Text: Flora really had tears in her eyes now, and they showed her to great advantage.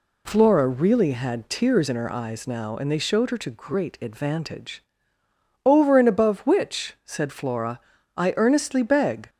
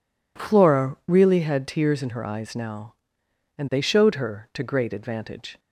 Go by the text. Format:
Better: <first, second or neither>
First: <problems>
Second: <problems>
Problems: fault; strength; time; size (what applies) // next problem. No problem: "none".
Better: second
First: goes on to say "Over and above which said Flora I earnestly beg"; strong; from 5.6 s on; 3.6 s long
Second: none